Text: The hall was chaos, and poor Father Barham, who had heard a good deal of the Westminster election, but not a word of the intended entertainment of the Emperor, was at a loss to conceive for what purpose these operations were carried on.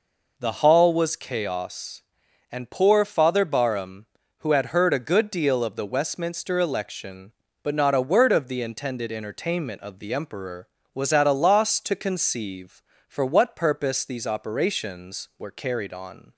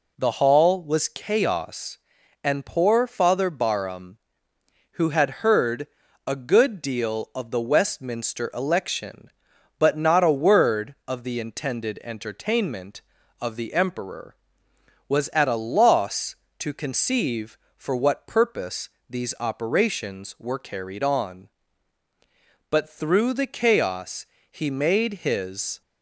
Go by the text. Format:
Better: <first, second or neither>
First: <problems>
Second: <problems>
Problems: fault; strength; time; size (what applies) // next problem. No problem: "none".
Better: first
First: none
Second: pauses between "heard" and "a"; at 5.8 s; 0.40 s long // pauses between "purpose" and "these"; slight; at 18.8 s; 0.20 s long // goes on to say "But through the chaos he made his"; strong; from 22.6 s on; 3.1 s long